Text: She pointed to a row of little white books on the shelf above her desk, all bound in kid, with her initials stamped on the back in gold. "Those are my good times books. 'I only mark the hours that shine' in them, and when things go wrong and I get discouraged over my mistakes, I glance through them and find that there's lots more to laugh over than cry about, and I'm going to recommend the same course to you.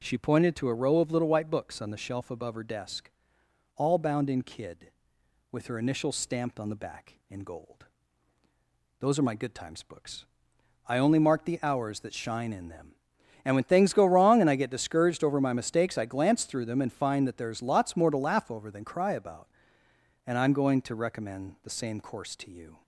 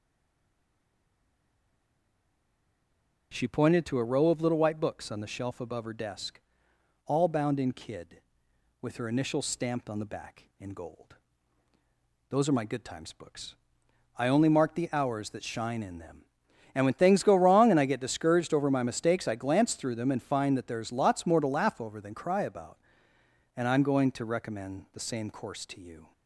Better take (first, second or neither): first